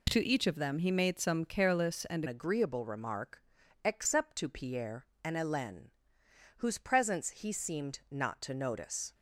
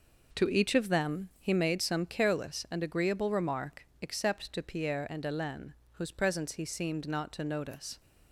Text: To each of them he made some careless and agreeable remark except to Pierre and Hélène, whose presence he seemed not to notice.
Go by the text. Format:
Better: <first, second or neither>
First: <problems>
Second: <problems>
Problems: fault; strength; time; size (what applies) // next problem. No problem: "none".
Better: second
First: changes voice at "agreeable"; from 2.2 s on; 6.9 s long // pauses between "remark" and "except"; at 3.4 s; 0.42 s long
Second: none